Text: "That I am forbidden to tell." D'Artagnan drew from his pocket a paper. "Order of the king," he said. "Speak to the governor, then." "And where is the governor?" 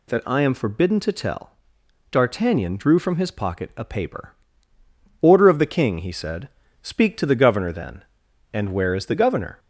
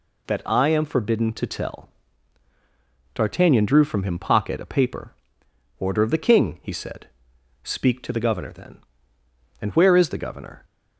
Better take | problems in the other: first | says "him" for "his"; at 4.0 s

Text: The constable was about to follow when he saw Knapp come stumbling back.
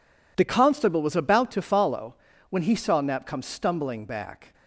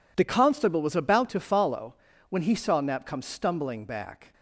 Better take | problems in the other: neither | pauses between "follow" and "when"; slight; the same in both

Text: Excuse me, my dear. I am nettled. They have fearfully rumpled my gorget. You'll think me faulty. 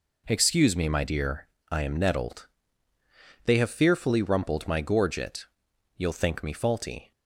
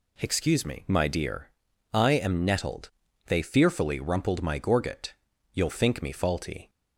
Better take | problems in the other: first | skips "have"; at 3.4 s

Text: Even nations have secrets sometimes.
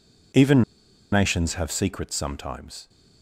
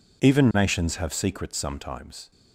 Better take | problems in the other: second | pauses between "Even" and "nations"; noticeable; at 0.6 s; 0.49 s long

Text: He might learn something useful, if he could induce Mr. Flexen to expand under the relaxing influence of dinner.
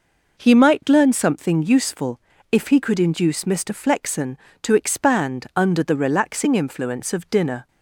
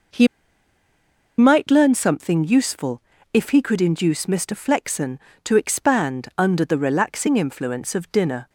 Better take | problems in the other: first | pauses between "He" and "might"; at 0.2 s; 1.1 s long

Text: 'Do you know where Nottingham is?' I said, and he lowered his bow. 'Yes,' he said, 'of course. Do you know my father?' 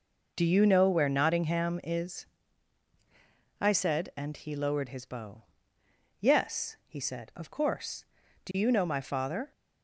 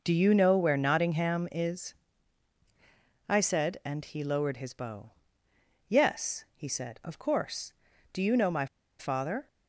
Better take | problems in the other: first | pauses between "my" and "father"; slight; at 8.6 s; 0.32 s long

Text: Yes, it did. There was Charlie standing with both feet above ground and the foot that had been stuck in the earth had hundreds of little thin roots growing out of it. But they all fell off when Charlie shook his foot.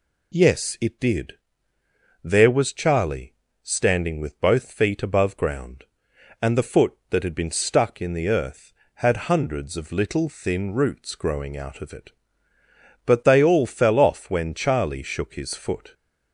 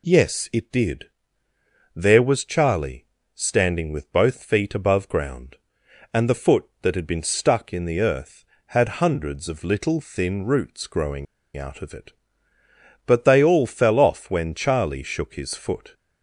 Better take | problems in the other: first | pauses between "Charlie" and "standing"; slight; at 3.0 s; 0.28 s long; slight in the first // pauses between "growing" and "out"; slight; at 11.2 s; 0.30 s long

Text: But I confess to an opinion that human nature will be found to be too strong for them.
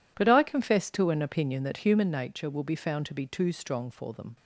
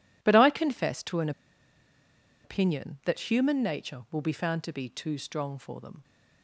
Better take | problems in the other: first | pauses between "an" and "opinion"; at 1.3 s; 1.1 s long

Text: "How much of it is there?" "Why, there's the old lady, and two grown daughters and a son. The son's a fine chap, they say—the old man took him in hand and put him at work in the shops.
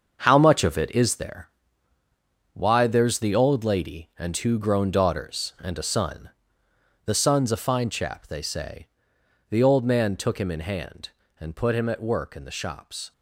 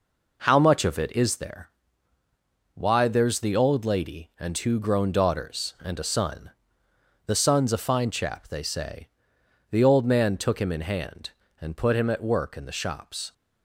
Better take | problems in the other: second | gets quieter; strong; throughout; 9 dB

